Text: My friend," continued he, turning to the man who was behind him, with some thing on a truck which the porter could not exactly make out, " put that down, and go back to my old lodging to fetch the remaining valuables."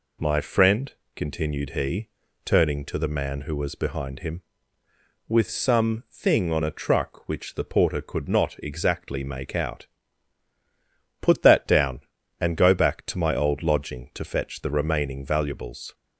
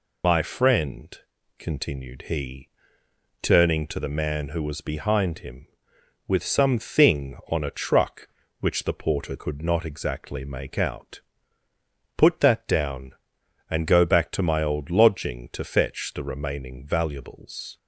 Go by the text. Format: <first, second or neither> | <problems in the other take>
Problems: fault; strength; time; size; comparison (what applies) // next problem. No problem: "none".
first | loses the start of "My"; at 0.2 s; 85 ms